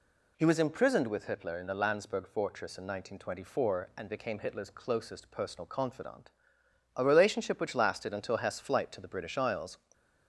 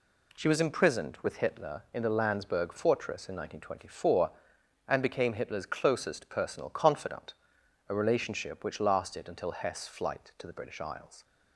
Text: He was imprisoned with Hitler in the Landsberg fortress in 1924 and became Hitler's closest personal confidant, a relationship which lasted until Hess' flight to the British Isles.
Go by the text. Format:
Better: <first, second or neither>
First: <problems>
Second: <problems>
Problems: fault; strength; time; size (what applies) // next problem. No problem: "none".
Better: first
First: none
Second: says "She" for "He"; at 0.3 s